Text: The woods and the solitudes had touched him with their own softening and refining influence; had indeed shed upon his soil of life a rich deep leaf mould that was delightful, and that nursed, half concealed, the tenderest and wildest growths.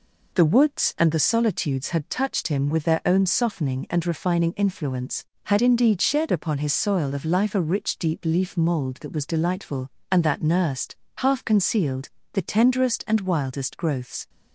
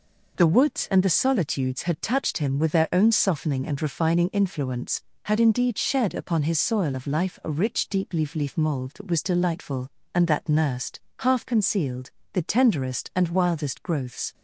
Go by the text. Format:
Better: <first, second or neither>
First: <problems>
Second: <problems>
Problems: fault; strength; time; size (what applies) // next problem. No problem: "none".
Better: first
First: none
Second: says "leaf" twice; at 8.3 s